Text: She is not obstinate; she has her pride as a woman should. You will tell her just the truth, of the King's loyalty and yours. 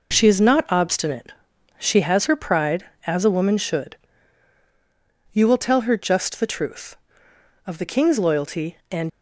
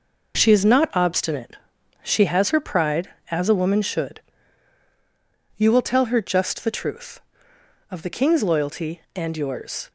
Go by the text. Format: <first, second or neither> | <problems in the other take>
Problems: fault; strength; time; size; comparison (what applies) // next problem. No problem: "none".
second | stops before "yours"; at 9.0 s